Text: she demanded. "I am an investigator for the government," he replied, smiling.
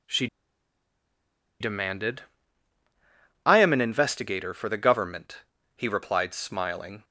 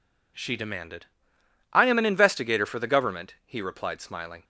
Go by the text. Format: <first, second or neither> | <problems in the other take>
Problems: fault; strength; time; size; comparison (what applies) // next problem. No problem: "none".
second | pauses between "she" and "demanded"; strong; at 0.2 s; 1.3 s long